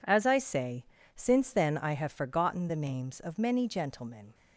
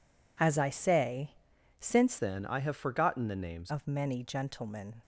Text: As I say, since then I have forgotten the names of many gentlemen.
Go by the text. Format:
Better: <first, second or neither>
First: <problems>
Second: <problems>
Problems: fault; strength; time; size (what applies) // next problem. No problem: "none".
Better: first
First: none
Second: changes voice from "then" to "names"; from 2.1 to 3.7 s; 1.6 s long